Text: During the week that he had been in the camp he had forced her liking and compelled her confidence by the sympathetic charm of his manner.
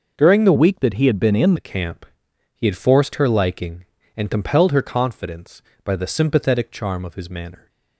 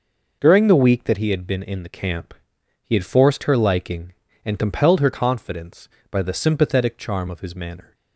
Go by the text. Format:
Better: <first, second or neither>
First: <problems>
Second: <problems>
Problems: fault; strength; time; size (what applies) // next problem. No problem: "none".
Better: second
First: changes voice from "week" to "in"; from 0.5 to 1.5 s; 1.0 s long // pauses between "camp" and "he"; noticeable; at 2.0 s; 0.50 s long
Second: pauses between "camp" and "he"; noticeable; at 2.3 s; 0.50 s long